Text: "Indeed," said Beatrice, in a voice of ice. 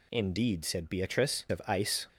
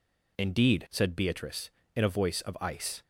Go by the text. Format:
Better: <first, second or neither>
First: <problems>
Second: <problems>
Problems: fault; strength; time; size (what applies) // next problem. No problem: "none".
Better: second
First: skips "in a voice"; at 1.4 s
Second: none